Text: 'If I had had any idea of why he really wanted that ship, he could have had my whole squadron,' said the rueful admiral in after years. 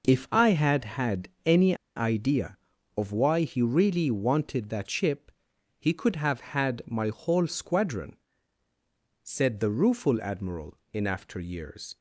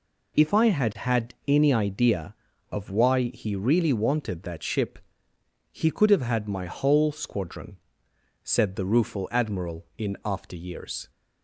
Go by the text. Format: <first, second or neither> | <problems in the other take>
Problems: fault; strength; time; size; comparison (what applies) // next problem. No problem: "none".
second | pauses between "had" and "any"; slight; at 1.2 s; 0.16 s long // pauses between "any" and "idea"; slight; at 1.7 s; 0.20 s long